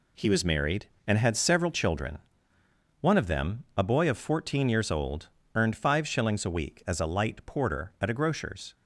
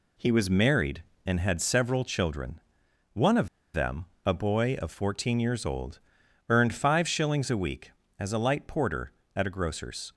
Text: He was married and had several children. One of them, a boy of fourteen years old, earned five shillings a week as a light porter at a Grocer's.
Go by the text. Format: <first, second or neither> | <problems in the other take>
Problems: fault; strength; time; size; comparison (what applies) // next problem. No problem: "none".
first | pauses between "of" and "them"; slight; at 3.4 s; 0.26 s long